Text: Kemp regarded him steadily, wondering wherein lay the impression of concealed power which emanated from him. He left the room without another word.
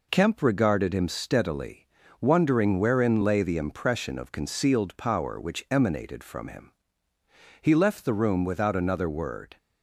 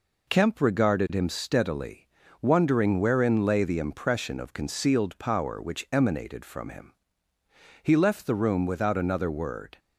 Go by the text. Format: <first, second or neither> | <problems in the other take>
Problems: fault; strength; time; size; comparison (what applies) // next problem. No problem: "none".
neither | none